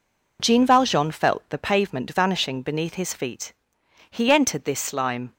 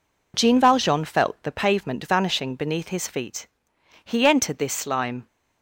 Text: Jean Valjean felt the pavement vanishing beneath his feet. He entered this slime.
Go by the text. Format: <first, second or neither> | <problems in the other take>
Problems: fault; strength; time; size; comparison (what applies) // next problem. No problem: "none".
neither | none